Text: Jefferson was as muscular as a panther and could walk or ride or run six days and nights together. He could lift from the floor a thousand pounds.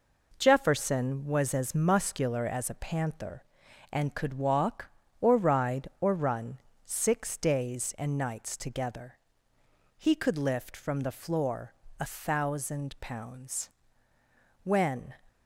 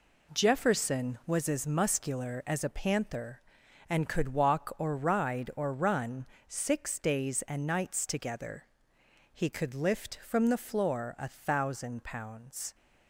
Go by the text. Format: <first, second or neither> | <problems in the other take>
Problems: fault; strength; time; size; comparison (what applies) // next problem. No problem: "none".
second | pauses between "run" and "six"; slight; at 6.5 s; 0.26 s long; slight in the second // pauses between "floor" and "a"; slight; at 11.7 s; 0.24 s long // goes on to say "When"; from 14.6 s on; 0.50 s long